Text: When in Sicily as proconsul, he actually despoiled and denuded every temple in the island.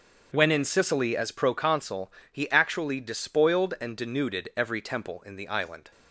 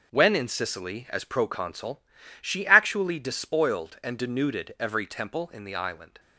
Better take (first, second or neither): first